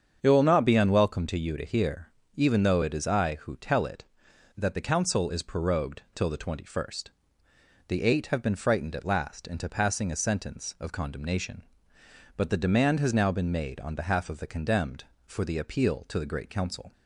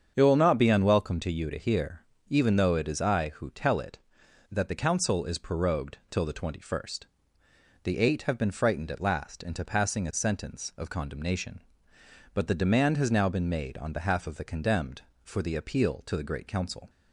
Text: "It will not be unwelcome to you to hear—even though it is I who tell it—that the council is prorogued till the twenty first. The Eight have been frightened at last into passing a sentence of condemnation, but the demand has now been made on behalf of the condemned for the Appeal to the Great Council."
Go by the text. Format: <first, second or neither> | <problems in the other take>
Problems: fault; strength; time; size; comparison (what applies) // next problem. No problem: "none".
neither | starts louder than the rest; strong; the same in both